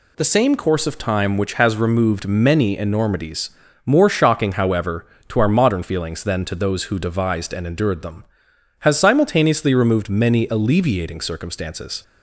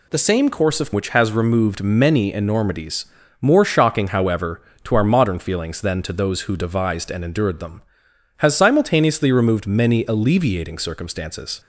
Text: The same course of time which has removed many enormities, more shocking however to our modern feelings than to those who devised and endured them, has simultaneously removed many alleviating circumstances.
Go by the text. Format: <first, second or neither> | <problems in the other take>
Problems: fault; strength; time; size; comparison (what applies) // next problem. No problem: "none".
first | skips "time"; at 0.9 s